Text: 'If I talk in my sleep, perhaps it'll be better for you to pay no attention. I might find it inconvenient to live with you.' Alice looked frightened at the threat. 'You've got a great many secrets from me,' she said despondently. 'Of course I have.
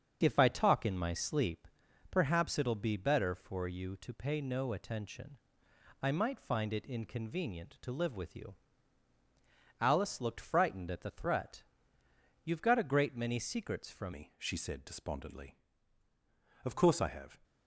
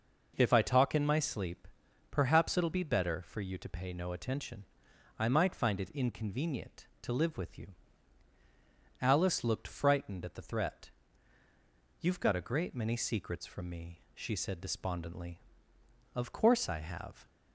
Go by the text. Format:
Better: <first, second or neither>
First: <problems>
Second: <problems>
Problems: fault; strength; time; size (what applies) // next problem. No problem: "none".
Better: second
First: starts louder than the rest; until 1.2 s; 6.5 dB // changes voice at "me"; from 14.1 s on; 3.2 s long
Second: none